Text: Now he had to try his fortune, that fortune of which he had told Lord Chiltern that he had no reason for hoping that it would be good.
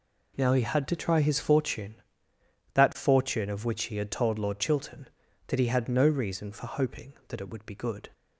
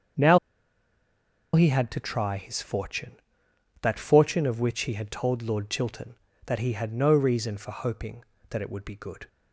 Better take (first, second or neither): first